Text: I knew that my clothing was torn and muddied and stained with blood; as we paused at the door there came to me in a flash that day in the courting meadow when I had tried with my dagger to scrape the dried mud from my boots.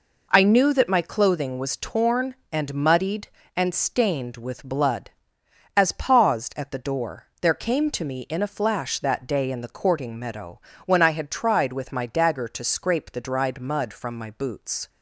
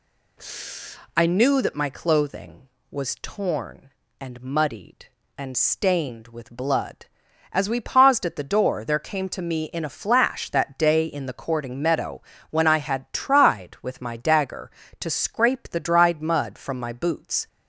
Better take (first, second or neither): second